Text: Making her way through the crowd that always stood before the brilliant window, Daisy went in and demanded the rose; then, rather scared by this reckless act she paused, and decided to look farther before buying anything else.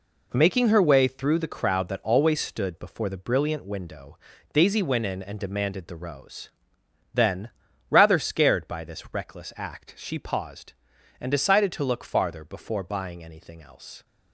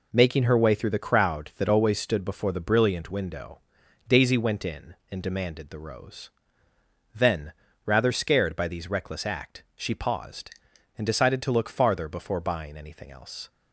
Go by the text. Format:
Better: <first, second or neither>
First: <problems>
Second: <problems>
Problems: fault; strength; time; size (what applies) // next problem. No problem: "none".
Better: first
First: none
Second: says "these" for "this"; at 8.6 s